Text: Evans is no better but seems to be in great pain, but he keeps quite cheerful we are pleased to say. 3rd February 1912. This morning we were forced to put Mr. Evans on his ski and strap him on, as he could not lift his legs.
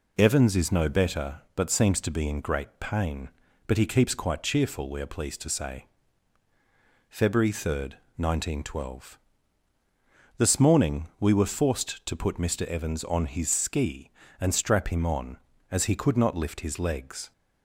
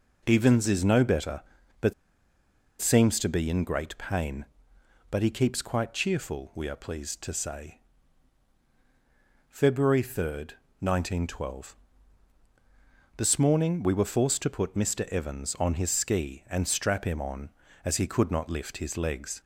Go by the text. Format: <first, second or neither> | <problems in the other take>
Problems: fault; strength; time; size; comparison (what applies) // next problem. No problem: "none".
first | pauses between "but" and "seems"; noticeable; at 1.9 s; 0.88 s long